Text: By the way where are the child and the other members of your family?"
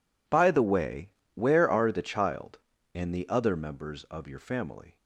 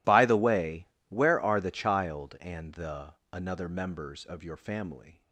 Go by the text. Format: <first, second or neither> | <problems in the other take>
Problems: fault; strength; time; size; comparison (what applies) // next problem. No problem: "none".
first | pauses between "way" and "where"; slight; at 0.8 s; 0.24 s long; slight in the first // says "another" for "other"; at 3.3 s